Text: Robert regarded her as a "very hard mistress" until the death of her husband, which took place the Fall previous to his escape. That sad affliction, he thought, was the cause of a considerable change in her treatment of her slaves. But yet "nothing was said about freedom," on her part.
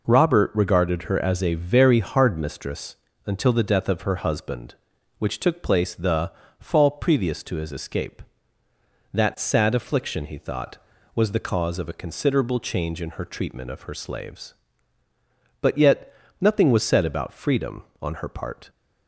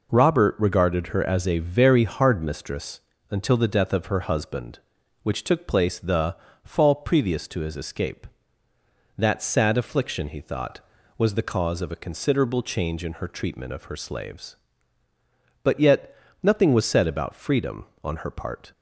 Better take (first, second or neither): neither